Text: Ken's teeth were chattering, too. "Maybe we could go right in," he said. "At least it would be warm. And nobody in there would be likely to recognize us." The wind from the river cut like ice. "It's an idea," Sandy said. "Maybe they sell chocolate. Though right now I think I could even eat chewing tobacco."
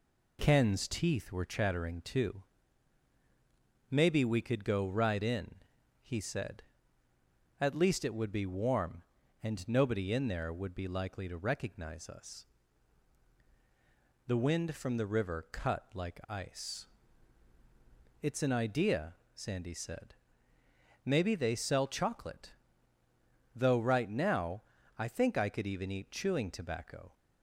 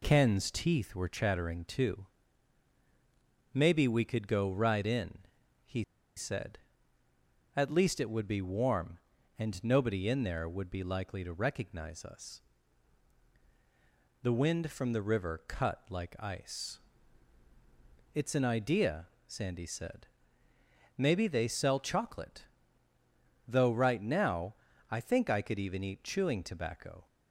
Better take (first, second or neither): first